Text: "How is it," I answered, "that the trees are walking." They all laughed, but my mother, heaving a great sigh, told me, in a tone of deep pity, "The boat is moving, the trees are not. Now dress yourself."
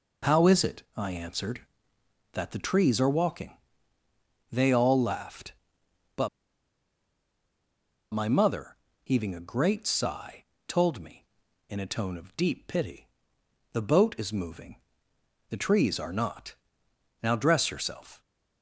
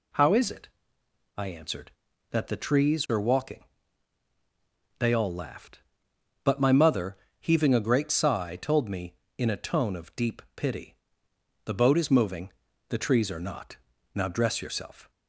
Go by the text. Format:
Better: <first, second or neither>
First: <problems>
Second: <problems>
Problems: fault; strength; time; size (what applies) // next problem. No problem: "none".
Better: second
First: pauses between "but" and "my"; strong; at 6.2 s; 1.8 s long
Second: none